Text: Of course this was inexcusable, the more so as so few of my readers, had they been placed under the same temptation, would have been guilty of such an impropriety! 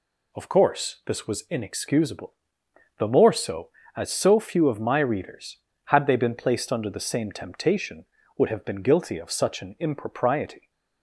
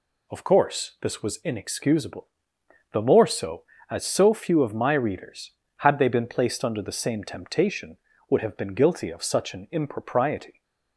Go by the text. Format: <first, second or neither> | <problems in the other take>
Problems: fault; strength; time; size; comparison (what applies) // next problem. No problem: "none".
neither | none